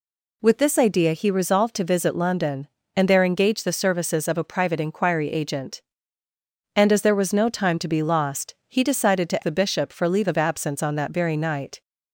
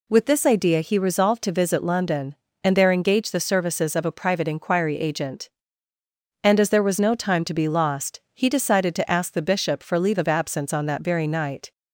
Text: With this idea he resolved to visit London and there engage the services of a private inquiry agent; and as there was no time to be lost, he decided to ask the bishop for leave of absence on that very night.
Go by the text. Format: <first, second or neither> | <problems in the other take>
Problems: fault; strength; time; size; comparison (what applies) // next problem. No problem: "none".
second | skips "ask"; at 9.4 s